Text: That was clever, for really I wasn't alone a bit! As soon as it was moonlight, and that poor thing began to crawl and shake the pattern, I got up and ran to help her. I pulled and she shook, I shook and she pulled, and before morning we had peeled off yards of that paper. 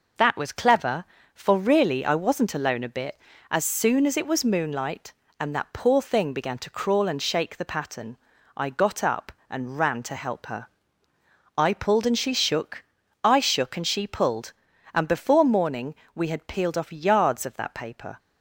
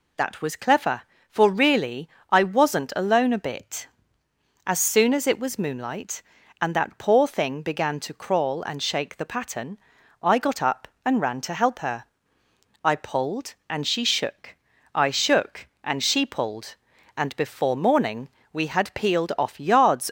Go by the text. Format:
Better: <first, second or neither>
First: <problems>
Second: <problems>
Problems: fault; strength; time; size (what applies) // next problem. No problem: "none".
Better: first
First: pauses between "morning" and "we"; slight; at 15.9 s; 0.20 s long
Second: pauses between "really" and "I"; slight; at 2.0 s; 0.22 s long // pauses between "morning" and "we"; slight; at 18.2 s; 0.24 s long // stops before "of that paper"; at 20.0 s